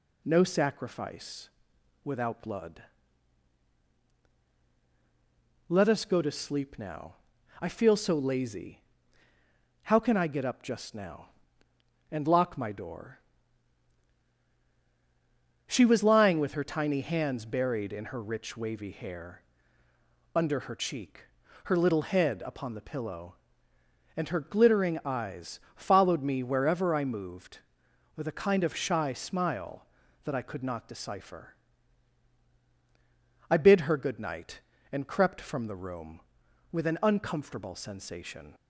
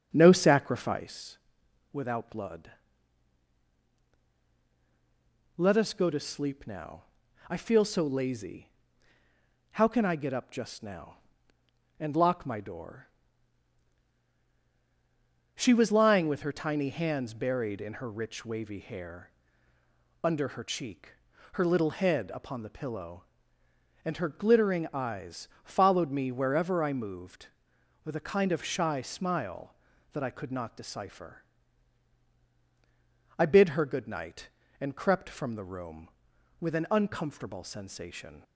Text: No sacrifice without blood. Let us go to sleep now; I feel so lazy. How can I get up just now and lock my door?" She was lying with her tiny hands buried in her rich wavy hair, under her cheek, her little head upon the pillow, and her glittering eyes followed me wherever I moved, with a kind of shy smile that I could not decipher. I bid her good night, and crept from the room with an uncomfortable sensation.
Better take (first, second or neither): first